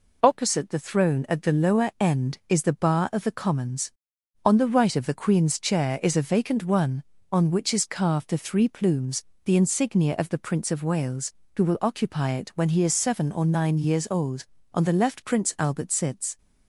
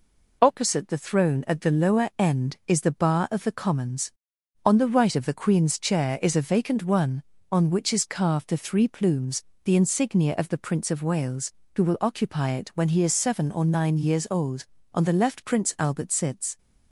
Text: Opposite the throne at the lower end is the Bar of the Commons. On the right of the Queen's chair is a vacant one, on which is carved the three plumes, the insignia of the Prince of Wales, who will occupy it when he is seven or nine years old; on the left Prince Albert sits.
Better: neither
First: none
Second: none

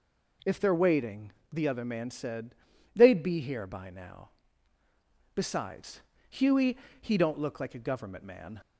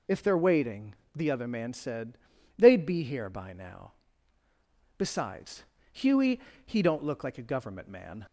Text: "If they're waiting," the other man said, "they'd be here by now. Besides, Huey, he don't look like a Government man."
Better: first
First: none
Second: loses the start of "If"; at 0.0 s; 25 ms

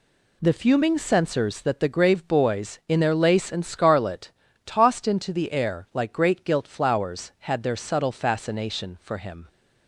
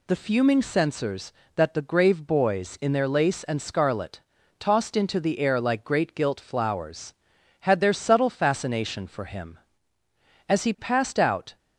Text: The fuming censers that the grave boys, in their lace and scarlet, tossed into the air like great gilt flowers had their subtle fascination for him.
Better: first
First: none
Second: goes on to say "As he passed out"; noticeable; from 10.4 s on; 1.0 s long

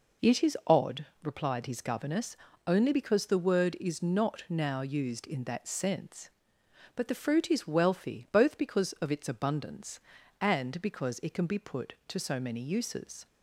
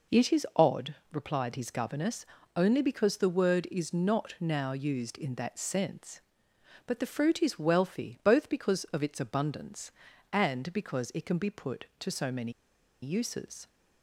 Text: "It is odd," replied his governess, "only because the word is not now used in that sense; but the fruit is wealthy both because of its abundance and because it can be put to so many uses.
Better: first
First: none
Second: pauses between "many" and "uses"; noticeable; at 12.5 s; 0.49 s long

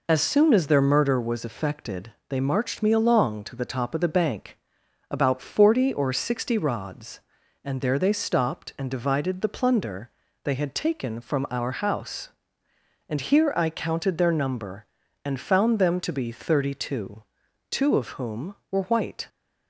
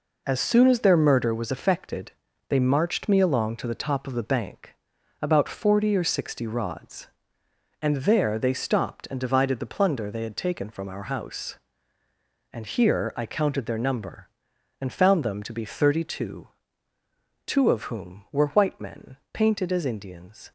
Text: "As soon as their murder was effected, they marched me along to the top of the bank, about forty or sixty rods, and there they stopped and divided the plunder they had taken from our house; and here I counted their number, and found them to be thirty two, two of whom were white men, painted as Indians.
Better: second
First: pauses between "plunder" and "they"; slight; at 10.0 s; 0.34 s long // stops before "men painted as Indians"; at 19.2 s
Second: none

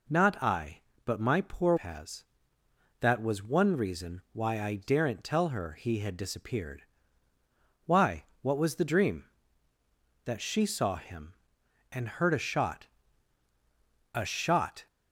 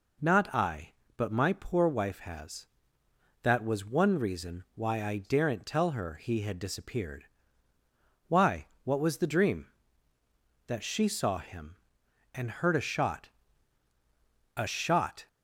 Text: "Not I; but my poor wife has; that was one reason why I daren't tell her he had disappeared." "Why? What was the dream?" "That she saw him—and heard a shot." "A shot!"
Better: second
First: skips "wife"; at 1.7 s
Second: none

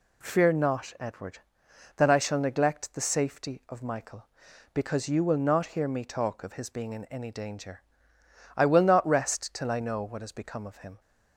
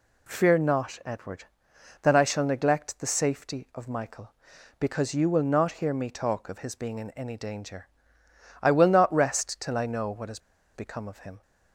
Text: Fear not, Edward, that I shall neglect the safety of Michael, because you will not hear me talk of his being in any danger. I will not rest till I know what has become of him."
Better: first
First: none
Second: pauses between "has" and "become"; slight; at 10.3 s; 0.35 s long

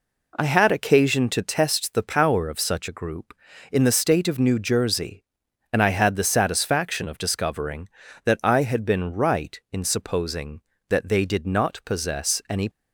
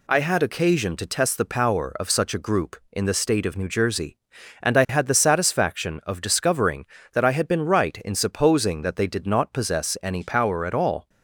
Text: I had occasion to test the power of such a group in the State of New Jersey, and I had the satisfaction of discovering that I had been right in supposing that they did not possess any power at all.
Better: second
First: stops before "power at all"; at 12.7 s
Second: none

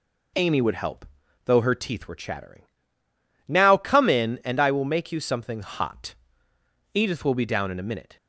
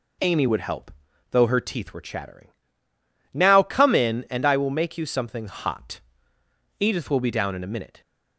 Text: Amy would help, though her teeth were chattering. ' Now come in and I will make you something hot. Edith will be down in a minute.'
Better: neither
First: none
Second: none

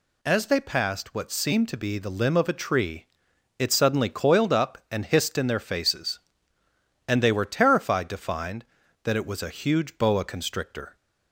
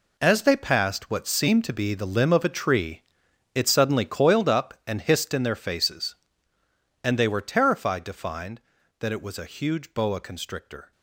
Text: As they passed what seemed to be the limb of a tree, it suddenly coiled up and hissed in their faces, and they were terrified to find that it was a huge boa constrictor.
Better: first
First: none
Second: gets quieter; strong; throughout; 11.5 dB

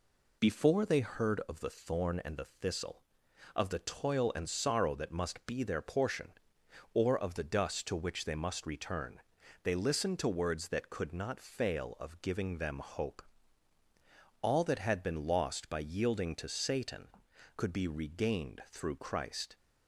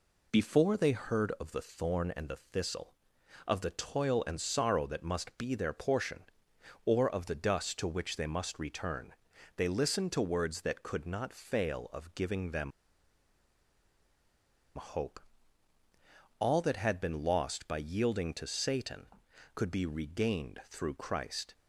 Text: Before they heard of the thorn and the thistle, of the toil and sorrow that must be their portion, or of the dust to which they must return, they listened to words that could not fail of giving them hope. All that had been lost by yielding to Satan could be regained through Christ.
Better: first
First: none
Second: pauses between "them" and "hope"; strong; at 12.7 s; 2.0 s long

